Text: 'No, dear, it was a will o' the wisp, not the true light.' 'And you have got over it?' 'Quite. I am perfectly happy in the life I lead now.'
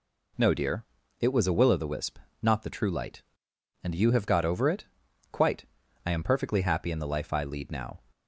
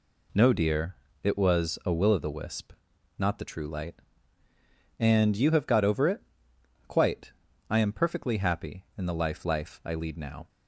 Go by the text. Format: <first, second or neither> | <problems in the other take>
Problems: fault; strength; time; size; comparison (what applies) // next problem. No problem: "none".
first | says "life" twice; at 9.4 s